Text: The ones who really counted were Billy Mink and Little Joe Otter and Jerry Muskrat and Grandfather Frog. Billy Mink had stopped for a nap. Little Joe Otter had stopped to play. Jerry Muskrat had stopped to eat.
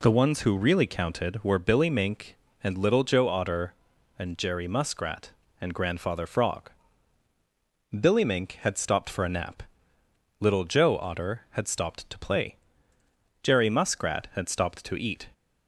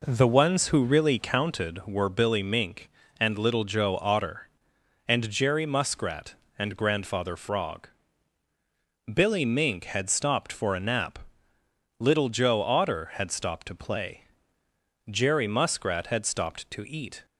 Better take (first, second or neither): first